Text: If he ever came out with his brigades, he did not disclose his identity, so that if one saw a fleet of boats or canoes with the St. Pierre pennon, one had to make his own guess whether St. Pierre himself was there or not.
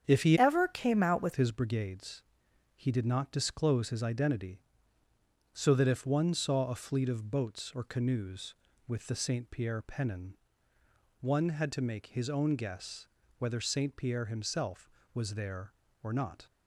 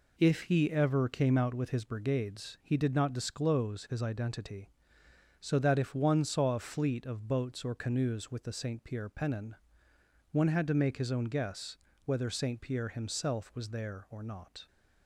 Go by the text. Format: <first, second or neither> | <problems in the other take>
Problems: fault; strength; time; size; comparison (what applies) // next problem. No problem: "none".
second | starts louder than the rest; strong; until 1.0 s; 8 dB // changes voice from "ever" to "with"; from 0.3 to 1.3 s; 1.0 s long // pauses between "guess" and "whether"; slight; at 13.0 s; 0.32 s long; slight in the second